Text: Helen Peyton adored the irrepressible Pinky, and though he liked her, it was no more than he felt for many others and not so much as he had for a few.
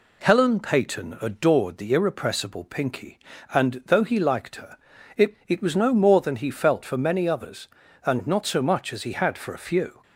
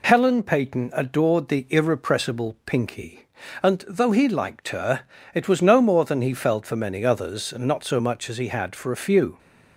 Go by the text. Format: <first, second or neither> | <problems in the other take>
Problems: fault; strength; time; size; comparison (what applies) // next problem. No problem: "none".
second | says "it" twice; at 5.4 s